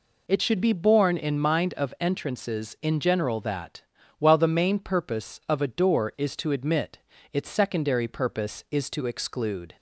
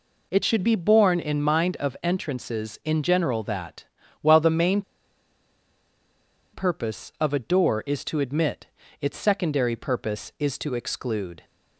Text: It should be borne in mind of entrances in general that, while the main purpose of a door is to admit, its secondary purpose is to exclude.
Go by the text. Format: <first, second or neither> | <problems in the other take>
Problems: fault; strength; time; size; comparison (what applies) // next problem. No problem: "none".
first | pauses between "main" and "purpose"; strong; at 4.8 s; 1.7 s long